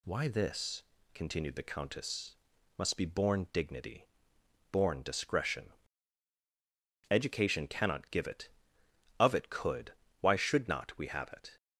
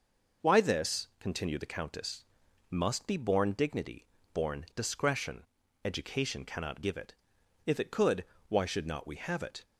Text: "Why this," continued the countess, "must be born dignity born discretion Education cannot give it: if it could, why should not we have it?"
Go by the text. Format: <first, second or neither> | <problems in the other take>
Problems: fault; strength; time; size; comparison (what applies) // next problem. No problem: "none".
second | pauses between "dignity" and "born"; noticeable; at 4.0 s; 0.64 s long; slight in the second // pauses between "discretion" and "Education"; strong; at 5.7 s; 1.3 s long; also in the second // says "of" for "if"; at 9.2 s